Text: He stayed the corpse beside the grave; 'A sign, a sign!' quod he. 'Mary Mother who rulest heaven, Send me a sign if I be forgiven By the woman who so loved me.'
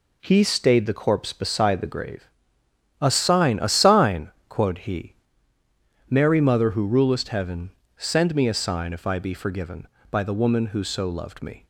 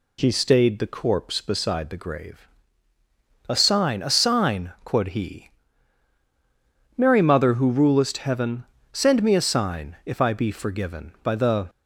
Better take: first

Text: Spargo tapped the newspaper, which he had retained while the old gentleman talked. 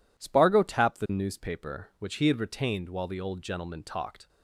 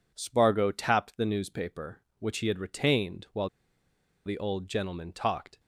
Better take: first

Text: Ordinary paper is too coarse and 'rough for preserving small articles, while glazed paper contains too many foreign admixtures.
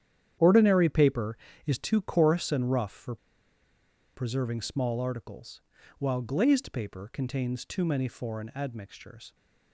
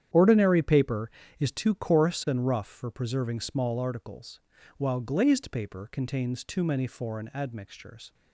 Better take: second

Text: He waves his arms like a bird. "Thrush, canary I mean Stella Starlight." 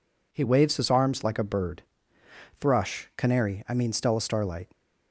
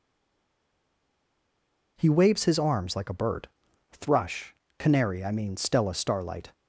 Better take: first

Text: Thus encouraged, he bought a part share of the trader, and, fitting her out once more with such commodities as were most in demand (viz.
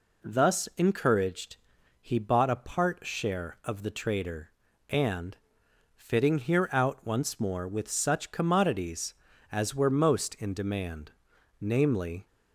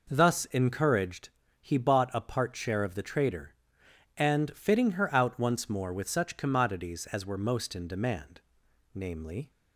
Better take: second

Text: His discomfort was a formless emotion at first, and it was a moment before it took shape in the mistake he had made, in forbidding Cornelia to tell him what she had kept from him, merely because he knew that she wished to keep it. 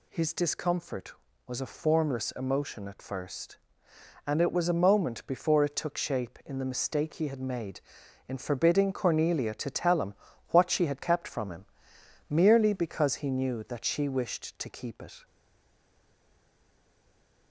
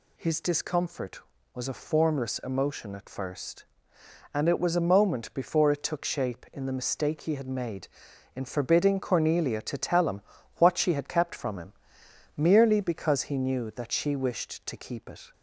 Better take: second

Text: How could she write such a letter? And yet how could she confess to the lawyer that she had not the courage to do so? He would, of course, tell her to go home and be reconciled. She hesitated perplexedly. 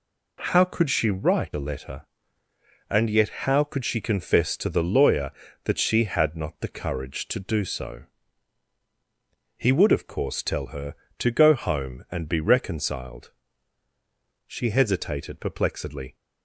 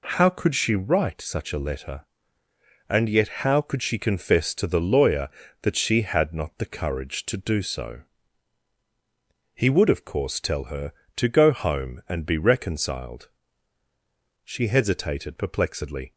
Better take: second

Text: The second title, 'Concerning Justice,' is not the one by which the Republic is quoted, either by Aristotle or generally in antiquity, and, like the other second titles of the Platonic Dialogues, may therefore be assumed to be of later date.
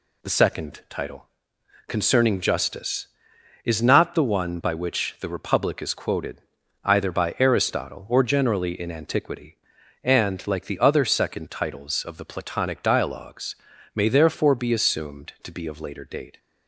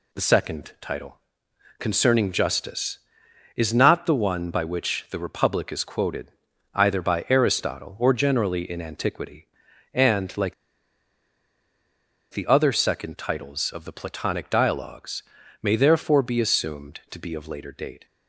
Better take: first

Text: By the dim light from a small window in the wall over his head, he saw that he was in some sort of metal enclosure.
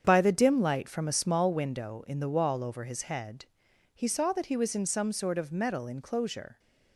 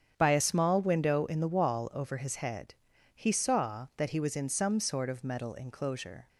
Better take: first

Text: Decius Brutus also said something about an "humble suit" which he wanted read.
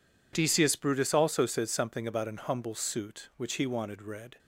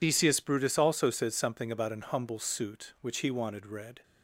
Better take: first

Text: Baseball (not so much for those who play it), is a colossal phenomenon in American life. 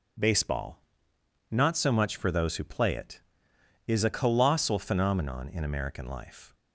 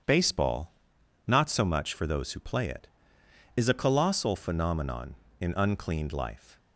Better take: first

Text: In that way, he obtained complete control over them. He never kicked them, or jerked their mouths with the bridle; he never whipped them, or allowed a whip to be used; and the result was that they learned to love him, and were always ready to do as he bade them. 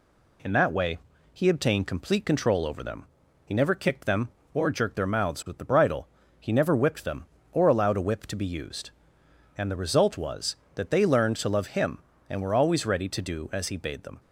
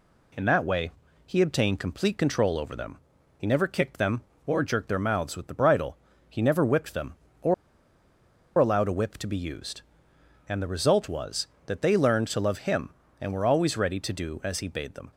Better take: first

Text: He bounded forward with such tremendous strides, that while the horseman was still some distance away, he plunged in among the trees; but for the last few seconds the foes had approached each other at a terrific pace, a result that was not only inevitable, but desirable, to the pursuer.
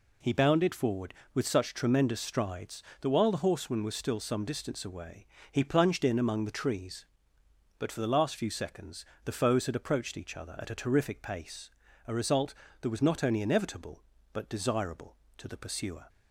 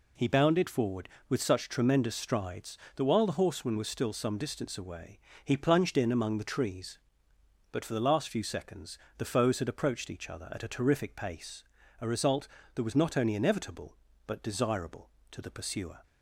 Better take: neither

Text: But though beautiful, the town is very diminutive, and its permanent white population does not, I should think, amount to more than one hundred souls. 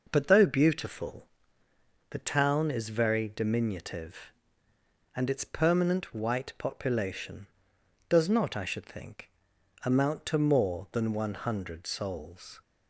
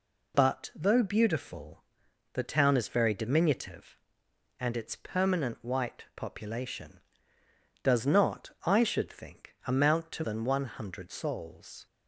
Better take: first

